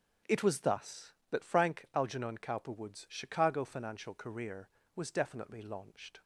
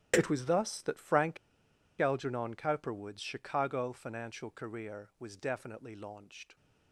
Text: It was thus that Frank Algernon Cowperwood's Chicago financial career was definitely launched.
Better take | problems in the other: first | starts louder than the rest; strong; until 1.1 s; 11.5 dB; also in the first // pauses between "Frank" and "Algernon"; noticeable; at 1.3 s; 0.63 s long

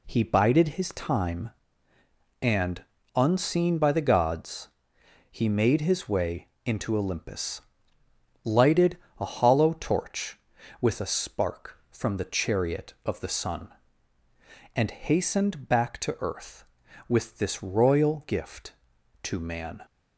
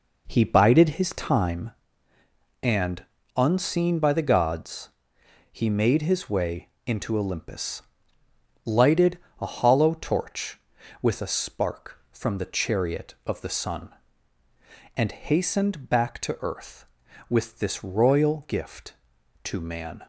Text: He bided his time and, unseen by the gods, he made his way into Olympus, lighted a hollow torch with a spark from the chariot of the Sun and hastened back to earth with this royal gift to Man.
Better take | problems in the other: first | starts louder than the rest; noticeable; until 1.6 s; 4.5 dB // pauses between "way" and "into"; slight; at 6.6 s; 0.16 s long; slight in the first // pauses between "lighted" and "a"; slight; at 9.1 s; 0.22 s long; slight in the first

